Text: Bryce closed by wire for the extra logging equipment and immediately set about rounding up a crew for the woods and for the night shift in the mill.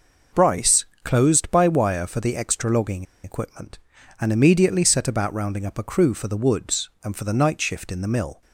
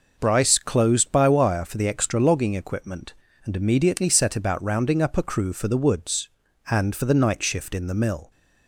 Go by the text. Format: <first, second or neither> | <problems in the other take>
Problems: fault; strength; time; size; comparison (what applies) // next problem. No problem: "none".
second | pauses between "Bryce" and "closed"; slight; at 0.8 s; 0.16 s long // pauses between "logging" and "equipment"; slight; at 3.0 s; 0.19 s long